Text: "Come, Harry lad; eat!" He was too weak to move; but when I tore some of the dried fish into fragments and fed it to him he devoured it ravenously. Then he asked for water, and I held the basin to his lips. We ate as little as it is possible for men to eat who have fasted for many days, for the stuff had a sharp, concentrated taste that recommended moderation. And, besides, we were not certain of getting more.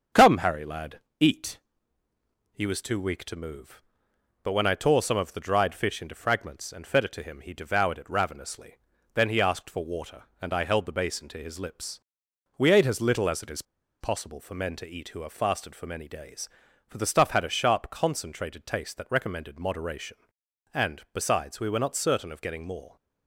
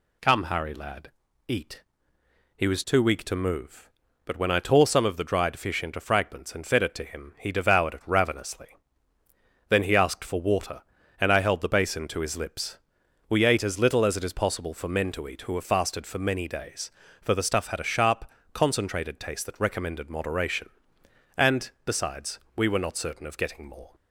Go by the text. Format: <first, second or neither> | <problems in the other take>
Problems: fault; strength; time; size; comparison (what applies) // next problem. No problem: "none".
second | starts louder than the rest; until 1.3 s; 7 dB // pauses between "is" and "possible"; at 13.6 s; 0.38 s long